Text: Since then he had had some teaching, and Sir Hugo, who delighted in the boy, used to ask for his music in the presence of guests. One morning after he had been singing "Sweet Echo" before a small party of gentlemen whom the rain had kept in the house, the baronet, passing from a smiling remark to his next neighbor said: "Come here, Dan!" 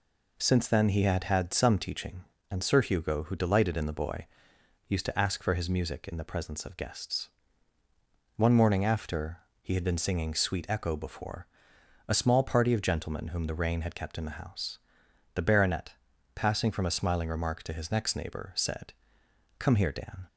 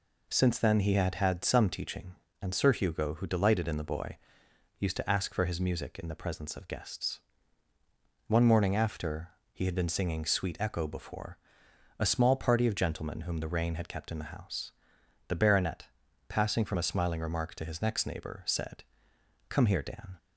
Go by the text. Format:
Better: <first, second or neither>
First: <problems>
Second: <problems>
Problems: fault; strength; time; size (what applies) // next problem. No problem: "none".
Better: neither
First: pauses between "after" and "he"; slight; at 9.3 s; 0.24 s long // pauses between "before" and "a"; noticeable; at 11.4 s; 0.60 s long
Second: pauses between "after" and "he"; slight; at 9.2 s; 0.24 s long // pauses between "before" and "a"; noticeable; at 11.3 s; 0.60 s long